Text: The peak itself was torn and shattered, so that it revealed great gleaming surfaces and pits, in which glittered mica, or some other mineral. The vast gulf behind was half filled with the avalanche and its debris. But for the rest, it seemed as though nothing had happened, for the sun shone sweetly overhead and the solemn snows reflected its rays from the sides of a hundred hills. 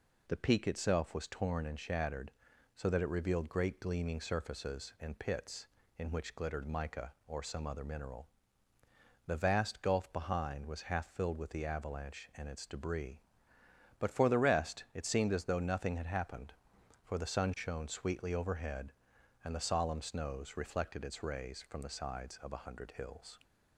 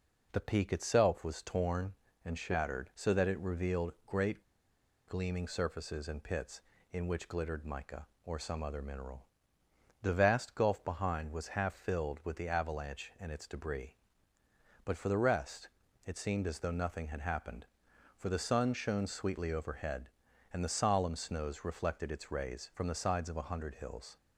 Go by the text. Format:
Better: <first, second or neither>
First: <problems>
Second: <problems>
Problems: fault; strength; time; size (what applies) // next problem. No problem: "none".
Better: first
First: none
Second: pauses between "great" and "gleaming"; noticeable; at 4.4 s; 0.65 s long